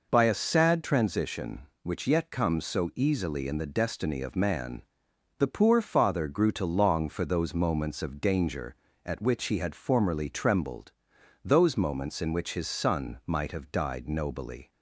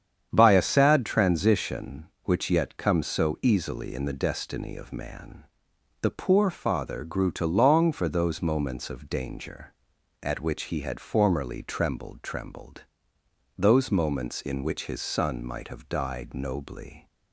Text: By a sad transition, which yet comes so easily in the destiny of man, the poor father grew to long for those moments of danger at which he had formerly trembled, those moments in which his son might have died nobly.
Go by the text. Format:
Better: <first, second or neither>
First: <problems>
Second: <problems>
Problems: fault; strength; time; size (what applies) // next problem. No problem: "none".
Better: first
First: none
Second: starts louder than the rest; strong; until 1.3 s; 8.5 dB // says "trembled" twice; at 12.2 s